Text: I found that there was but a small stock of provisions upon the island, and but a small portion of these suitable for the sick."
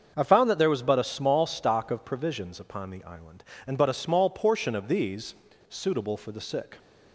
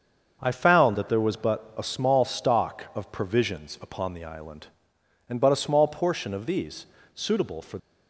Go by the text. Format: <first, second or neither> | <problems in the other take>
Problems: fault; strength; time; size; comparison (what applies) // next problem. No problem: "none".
first | starts louder than the rest; until 1.4 s; 6.5 dB; also in the first // pauses between "these" and "suitable"; slight; at 6.8 s; 0.28 s long; slight in the first // stops before "the sick"; at 7.7 s